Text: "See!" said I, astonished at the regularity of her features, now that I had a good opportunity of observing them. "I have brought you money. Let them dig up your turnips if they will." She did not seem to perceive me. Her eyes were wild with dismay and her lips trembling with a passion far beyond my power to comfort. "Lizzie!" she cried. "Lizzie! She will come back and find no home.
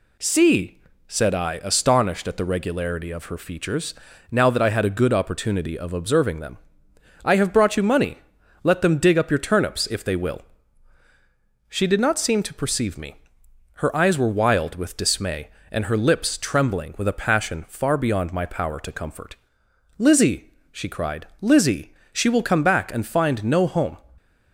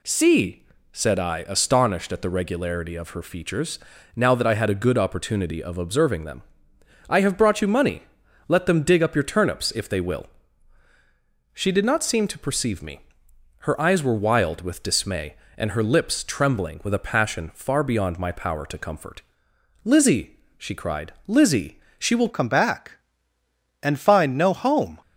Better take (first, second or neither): first